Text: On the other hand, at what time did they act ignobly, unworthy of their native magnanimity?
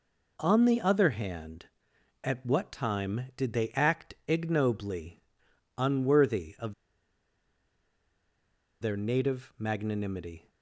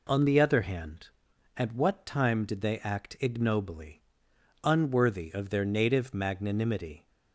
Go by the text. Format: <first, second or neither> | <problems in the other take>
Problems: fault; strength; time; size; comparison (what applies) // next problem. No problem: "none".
second | pauses between "of" and "their"; strong; at 6.7 s; 2.0 s long